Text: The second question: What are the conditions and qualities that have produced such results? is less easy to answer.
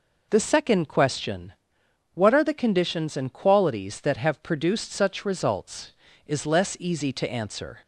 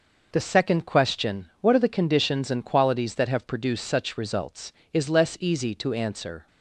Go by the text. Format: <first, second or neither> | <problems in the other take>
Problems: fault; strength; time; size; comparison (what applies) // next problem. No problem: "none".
neither | none